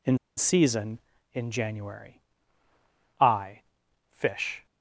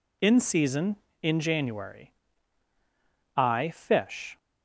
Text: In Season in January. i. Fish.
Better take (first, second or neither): second